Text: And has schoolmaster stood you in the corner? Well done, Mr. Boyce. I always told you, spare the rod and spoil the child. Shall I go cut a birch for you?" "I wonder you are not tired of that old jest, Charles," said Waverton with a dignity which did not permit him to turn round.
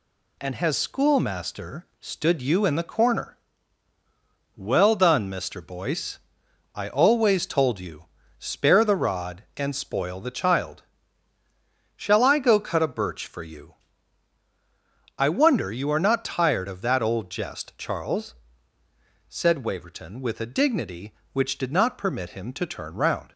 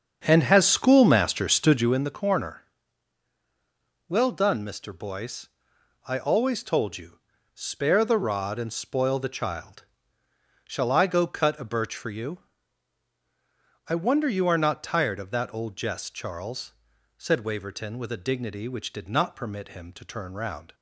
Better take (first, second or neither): first